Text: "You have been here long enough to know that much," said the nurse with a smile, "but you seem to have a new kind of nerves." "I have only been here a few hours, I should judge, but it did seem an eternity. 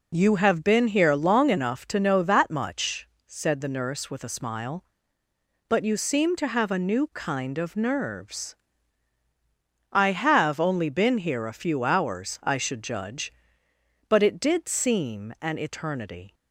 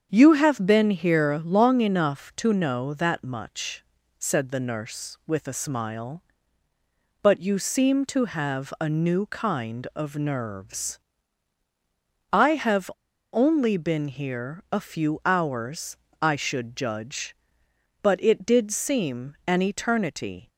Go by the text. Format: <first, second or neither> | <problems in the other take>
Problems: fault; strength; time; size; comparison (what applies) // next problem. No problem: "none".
first | starts louder than the rest; strong; until 1.1 s; 7.5 dB // pauses between "have" and "only"; at 12.9 s; 0.43 s long